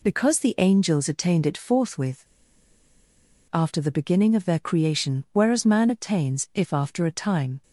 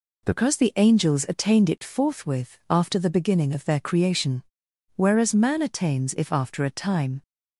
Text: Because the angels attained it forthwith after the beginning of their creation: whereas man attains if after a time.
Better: second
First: pauses between "forthwith" and "after"; strong; at 2.2 s; 1.2 s long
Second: none

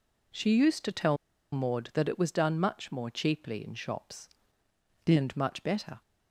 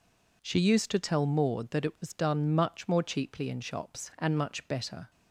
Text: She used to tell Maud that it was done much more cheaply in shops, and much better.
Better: second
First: pauses between "tell" and "Maud"; at 1.1 s; 0.36 s long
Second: none

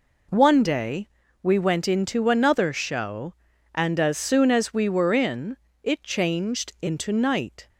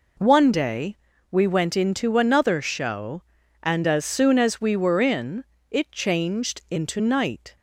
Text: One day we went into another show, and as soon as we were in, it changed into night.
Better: neither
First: pauses between "day" and "we"; slight; at 1.0 s; 0.34 s long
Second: pauses between "day" and "we"; slight; at 0.9 s; 0.34 s long

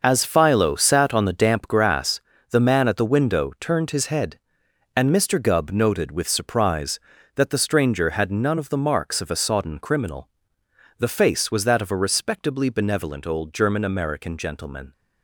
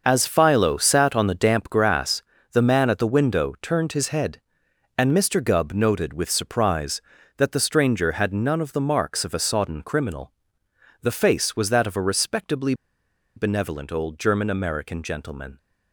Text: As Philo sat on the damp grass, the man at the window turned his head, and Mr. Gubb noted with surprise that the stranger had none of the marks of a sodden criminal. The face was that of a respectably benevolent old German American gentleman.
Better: first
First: starts louder than the rest; noticeable; until 1.0 s; 6 dB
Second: starts louder than the rest; noticeable; until 1.0 s; 6 dB // pauses between "respectably" and "benevolent"; noticeable; at 12.7 s; 0.62 s long

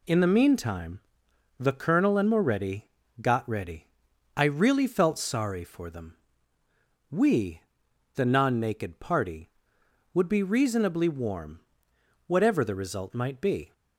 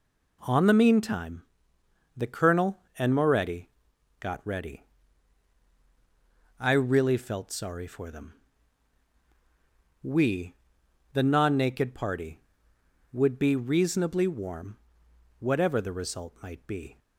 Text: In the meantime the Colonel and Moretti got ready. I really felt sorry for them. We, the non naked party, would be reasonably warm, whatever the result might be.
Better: first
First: pauses between "meantime" and "the"; noticeable; at 0.9 s; 0.62 s long // pauses between "Moretti" and "got"; slight; at 2.8 s; 0.32 s long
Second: says "On" for "In"; at 0.4 s // pauses between "meantime" and "the"; noticeable; at 1.4 s; 0.74 s long // pauses between "Moretti" and "got"; noticeable; at 3.6 s; 0.50 s long

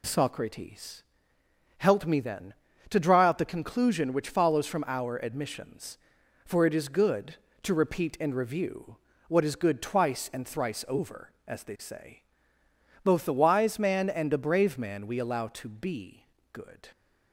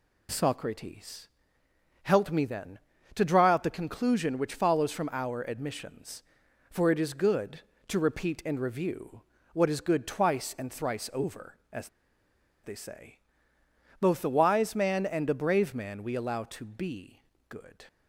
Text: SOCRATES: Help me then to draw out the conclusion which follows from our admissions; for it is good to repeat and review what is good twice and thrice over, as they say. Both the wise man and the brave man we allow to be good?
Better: first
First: pauses between "review" and "what"; slight; at 8.9 s; 0.30 s long // pauses between "be" and "good"; slight; at 16.2 s; 0.28 s long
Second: pauses between "review" and "what"; slight; at 9.2 s; 0.30 s long // pauses between "as" and "they"; noticeable; at 11.8 s; 0.75 s long // pauses between "be" and "good"; slight; at 17.2 s; 0.28 s long

